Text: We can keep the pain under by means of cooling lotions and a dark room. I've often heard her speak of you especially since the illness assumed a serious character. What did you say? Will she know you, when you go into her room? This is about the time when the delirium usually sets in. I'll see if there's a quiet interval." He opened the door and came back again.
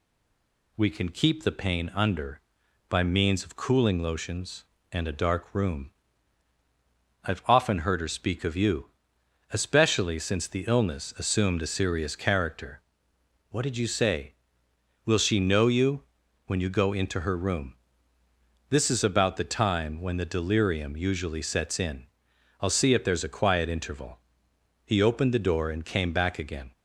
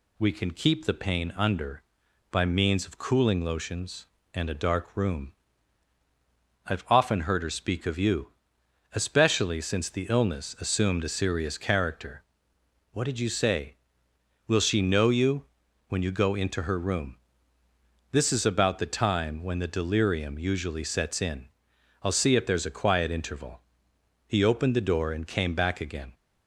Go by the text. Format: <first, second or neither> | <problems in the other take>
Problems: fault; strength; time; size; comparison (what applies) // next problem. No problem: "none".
second | stays silent before the first word; slight; until 0.7 s; 0.7 s long // pauses between "you" and "especially"; noticeable; at 8.8 s; 0.64 s long; noticeable in the second